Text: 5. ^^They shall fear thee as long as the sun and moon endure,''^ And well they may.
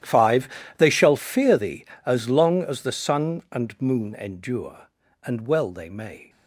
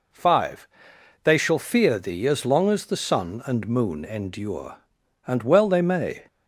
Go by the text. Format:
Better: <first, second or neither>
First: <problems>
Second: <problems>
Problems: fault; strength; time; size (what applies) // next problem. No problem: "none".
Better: second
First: gets quieter; strong; throughout; 18.5 dB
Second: none